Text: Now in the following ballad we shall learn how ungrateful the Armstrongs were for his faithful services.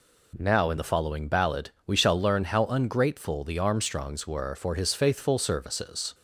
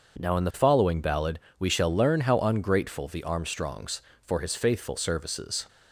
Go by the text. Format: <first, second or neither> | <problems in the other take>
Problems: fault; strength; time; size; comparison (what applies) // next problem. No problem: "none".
first | starts louder than the rest; until 1.2 s; 6.5 dB // pauses between "ballad" and "we"; slight; at 1.3 s; 0.18 s long // skips "were"; at 4.1 s